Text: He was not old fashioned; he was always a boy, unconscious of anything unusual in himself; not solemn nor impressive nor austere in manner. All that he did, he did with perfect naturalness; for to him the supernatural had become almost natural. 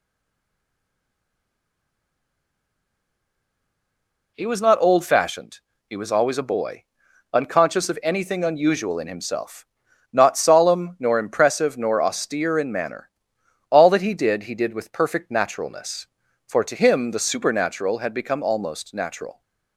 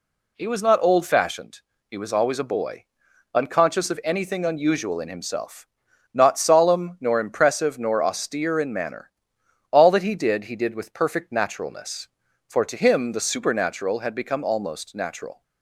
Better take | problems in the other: second | stays silent before the first word; strong; until 4.3 s; 4.3 s long

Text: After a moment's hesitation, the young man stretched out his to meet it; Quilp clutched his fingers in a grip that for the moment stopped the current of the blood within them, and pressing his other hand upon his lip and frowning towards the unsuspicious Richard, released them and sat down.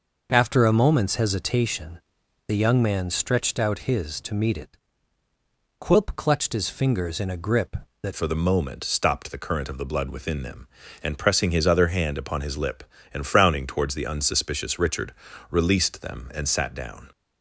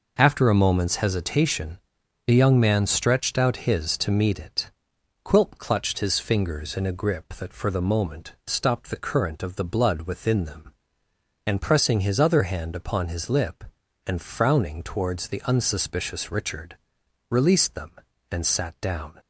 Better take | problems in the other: second | changes voice at "for"; from 8.1 s on; 9.0 s long

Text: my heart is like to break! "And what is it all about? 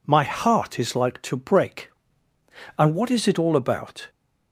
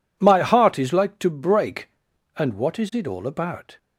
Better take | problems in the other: neither | none

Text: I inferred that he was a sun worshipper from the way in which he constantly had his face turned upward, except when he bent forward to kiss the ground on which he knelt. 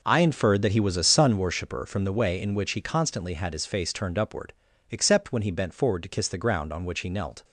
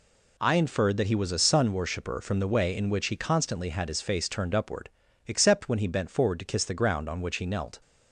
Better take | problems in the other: second | starts louder than the rest; noticeable; until 1.8 s; 5 dB

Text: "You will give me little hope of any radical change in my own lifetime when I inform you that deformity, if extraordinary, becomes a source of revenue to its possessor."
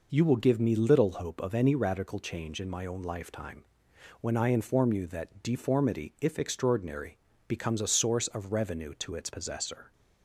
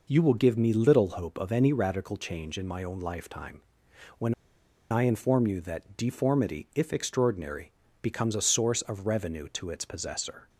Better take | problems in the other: first | pauses between "lifetime" and "when"; noticeable; at 3.6 s; 0.56 s long; noticeable in the first // pauses between "when" and "I"; noticeable; at 4.3 s; 0.58 s long

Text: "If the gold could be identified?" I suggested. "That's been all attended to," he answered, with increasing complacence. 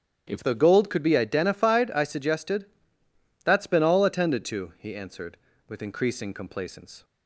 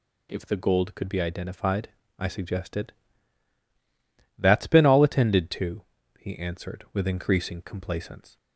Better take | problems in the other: second | starts louder than the rest; strong; until 1.2 s; 10 dB // changes voice at "the"; from 0.4 s on; 6.6 s long

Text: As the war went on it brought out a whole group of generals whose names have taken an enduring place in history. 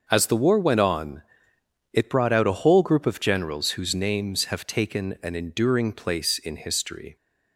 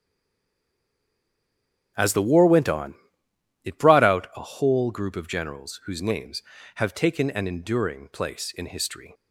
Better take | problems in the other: first | stays silent before the first word; noticeable; until 1.9 s; 1.9 s long // starts louder than the rest; strong; until 3.6 s; 8 dB; also in the first // pauses between "on" and "it"; noticeable; at 2.9 s; 0.70 s long; noticeable in the first

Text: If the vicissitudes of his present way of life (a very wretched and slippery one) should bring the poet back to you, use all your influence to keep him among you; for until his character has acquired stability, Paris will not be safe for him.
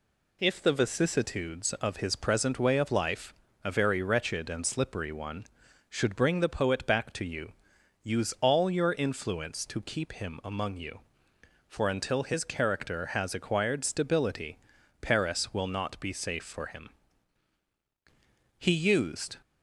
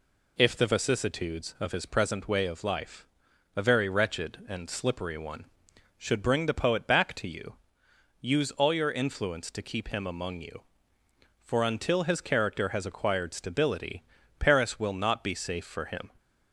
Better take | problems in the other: second | goes on to say "He used"; noticeable; from 18.5 s on; 0.78 s long

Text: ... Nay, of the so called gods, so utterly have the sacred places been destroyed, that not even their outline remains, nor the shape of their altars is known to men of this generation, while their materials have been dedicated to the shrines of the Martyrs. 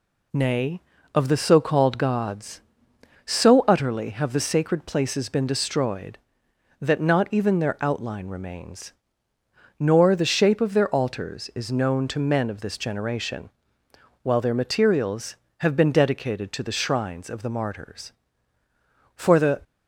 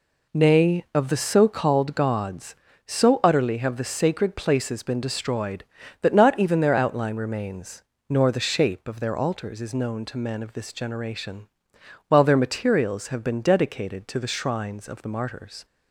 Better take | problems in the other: second | goes on to say "For the"; slight; from 19.1 s on; 0.44 s long

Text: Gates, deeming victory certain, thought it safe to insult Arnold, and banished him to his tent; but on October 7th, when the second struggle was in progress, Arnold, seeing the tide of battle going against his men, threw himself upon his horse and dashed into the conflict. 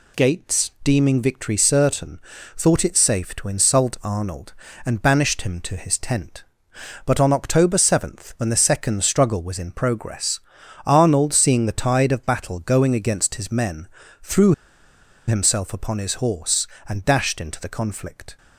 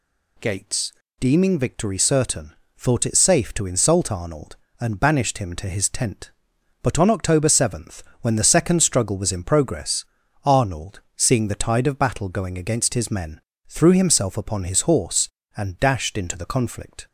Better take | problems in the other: second | pauses between "threw" and "himself"; noticeable; at 14.5 s; 0.73 s long

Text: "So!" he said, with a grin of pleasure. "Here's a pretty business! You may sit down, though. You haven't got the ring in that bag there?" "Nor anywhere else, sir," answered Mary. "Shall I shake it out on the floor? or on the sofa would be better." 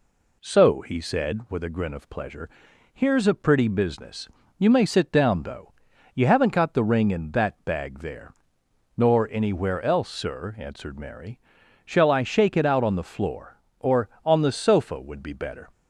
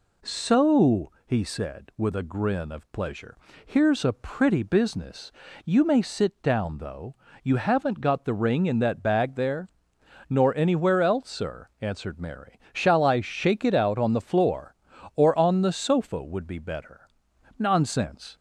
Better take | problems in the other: first | goes on to say "Nonsense"; noticeable; from 17.5 s on; 0.78 s long

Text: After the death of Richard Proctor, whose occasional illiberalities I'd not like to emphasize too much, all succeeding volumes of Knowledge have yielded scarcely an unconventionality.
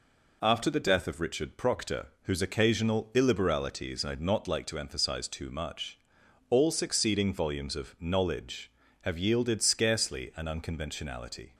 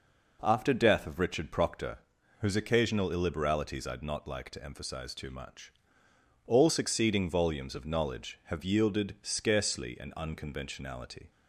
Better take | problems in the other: first | skips "the"; at 0.7 s

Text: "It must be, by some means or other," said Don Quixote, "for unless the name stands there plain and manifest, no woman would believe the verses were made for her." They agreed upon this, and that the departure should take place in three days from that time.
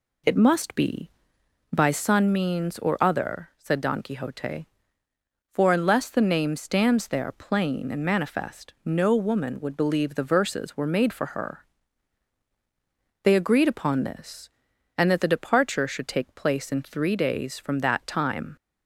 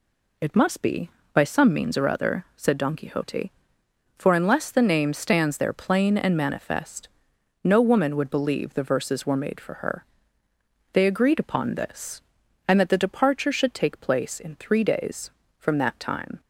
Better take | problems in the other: second | says "sun" for "some"; at 1.9 s

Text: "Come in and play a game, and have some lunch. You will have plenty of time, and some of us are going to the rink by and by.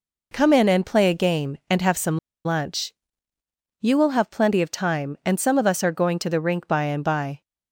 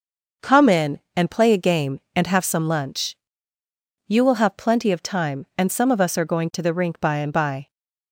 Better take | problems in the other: second | pauses between "some" and "lunch"; slight; at 2.1 s; 0.26 s long

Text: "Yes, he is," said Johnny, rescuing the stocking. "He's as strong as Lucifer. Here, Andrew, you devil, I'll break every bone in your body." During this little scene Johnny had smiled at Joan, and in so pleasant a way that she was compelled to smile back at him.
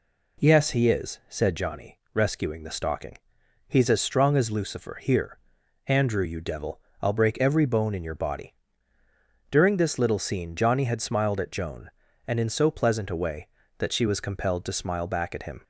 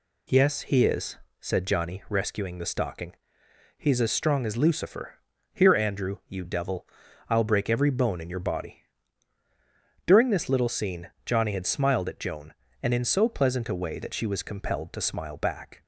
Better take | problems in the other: first | stops before "at him"; at 15.8 s

